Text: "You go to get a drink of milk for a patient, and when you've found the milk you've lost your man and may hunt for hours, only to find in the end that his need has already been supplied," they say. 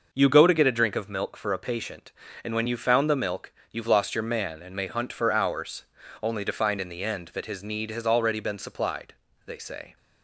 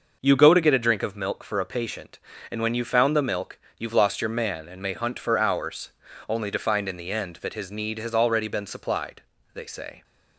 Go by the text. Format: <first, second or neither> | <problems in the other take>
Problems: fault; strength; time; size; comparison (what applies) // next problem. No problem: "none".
neither | pauses between "milk" and "you've"; slight; the same in both